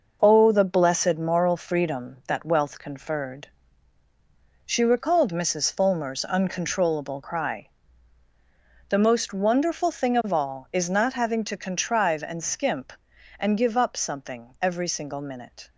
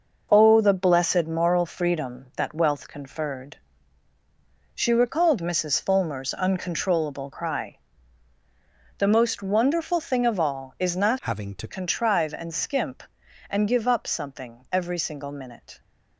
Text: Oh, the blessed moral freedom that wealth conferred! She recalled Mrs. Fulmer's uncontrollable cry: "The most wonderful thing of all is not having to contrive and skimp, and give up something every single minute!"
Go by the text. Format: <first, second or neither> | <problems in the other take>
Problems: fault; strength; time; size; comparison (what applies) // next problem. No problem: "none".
first | changes voice from "having" to "to"; from 11.2 to 11.6 s; 0.4 s long